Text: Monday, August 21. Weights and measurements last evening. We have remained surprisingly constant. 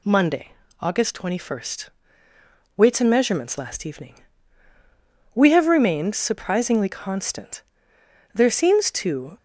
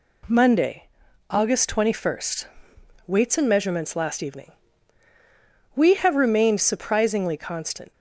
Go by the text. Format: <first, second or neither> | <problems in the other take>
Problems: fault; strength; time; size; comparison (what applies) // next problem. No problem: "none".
second | goes on to say "There seems to"; noticeable; from 8.3 s on; 1.0 s long